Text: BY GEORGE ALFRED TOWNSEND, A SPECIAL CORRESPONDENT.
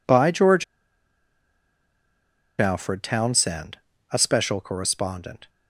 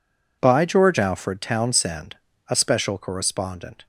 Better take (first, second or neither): second